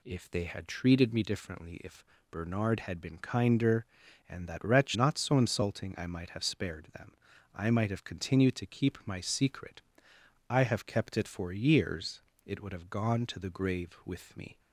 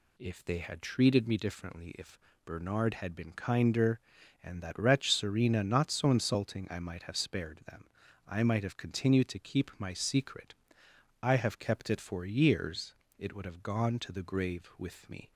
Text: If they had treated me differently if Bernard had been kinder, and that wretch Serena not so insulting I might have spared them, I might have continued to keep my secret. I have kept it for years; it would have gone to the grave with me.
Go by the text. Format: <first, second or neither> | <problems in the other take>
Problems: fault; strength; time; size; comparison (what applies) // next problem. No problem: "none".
second | pauses between "if" and "Bernard"; slight; at 2.0 s; 0.26 s long; slight in the second // skips "Serena"; at 4.9 s